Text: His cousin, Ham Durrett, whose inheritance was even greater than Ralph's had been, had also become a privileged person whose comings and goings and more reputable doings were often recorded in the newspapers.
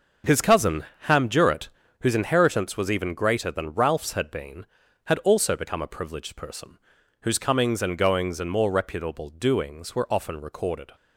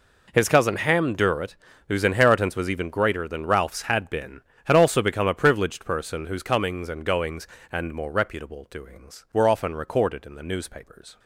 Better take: second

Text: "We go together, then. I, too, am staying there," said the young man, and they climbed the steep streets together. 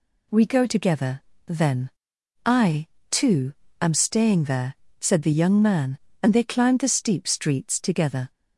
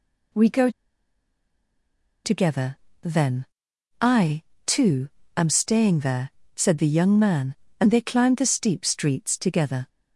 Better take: first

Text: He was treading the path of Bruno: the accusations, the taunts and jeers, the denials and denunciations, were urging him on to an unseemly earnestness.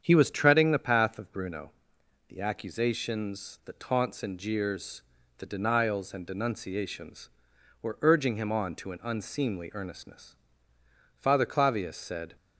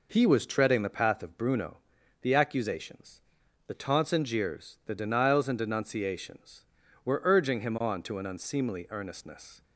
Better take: second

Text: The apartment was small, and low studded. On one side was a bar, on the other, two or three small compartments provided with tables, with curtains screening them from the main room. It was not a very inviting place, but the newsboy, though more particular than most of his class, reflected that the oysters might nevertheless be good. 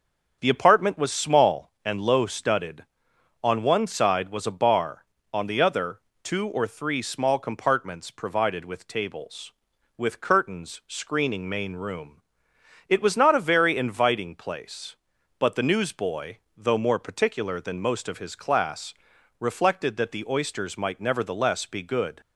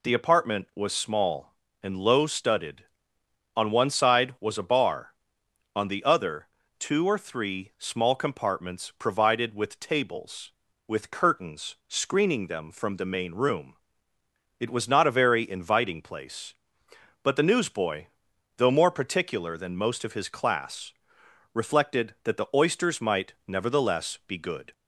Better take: second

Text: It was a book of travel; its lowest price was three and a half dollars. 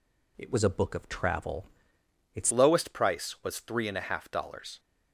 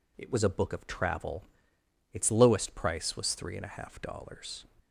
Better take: second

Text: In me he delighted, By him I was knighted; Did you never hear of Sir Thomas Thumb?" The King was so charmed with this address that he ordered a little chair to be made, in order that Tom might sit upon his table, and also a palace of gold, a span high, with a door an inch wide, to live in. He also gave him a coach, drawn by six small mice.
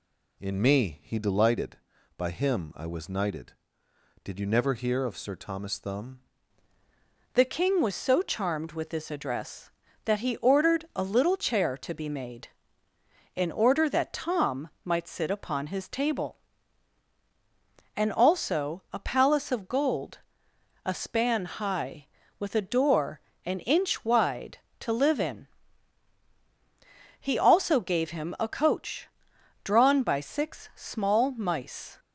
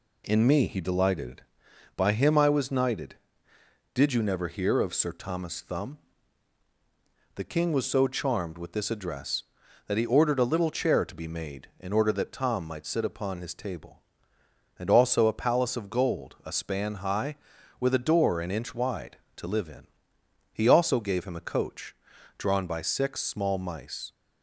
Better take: second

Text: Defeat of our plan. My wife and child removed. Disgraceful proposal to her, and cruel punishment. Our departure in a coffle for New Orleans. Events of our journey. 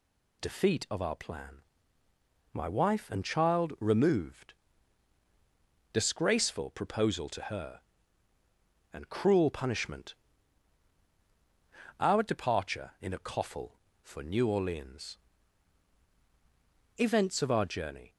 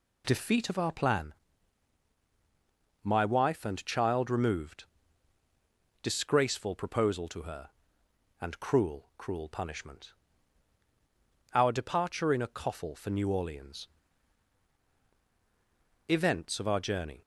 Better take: first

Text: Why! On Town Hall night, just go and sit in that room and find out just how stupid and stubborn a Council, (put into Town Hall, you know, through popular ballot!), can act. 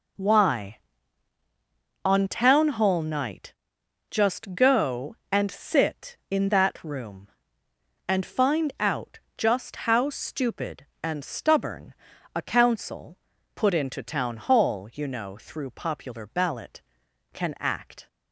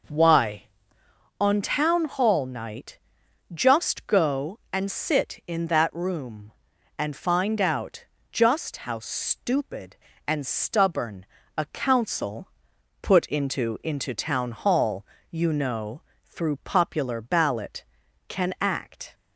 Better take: first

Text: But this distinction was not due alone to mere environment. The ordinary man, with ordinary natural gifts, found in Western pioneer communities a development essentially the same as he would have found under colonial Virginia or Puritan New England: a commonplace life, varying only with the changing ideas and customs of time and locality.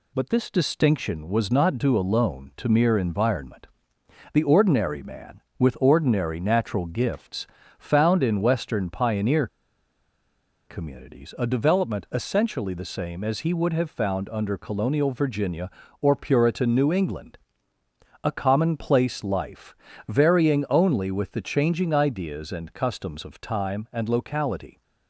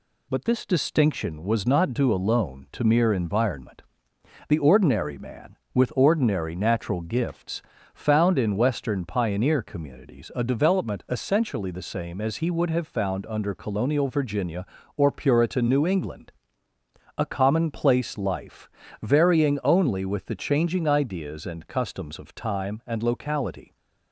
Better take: second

